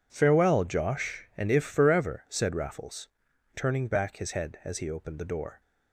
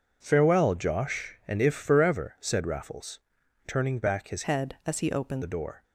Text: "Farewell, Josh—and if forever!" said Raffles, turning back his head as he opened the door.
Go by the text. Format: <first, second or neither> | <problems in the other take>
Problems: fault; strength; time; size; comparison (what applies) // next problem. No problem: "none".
first | changes voice from "head" to "opened"; from 4.4 to 5.4 s; 1.0 s long